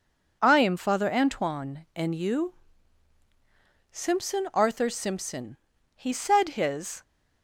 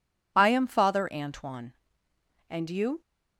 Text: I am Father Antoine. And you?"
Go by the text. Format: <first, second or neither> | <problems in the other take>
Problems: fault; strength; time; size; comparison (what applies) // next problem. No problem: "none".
second | goes on to say "Simpson Arthur Simpson He said his"; strong; from 3.8 s on; 3.1 s long